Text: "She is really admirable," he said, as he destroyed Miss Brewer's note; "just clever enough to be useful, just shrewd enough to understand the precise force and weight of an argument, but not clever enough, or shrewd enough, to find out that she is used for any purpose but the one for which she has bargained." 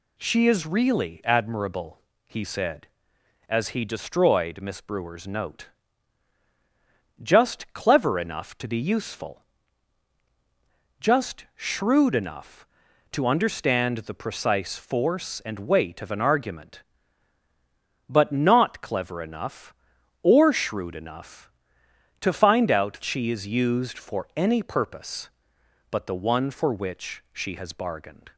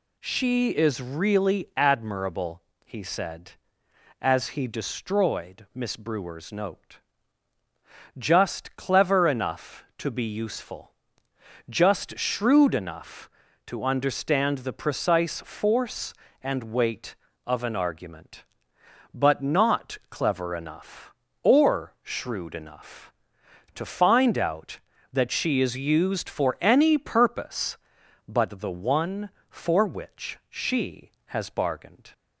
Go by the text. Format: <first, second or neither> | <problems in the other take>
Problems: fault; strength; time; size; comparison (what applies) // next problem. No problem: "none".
second | skips "that"; at 23.0 s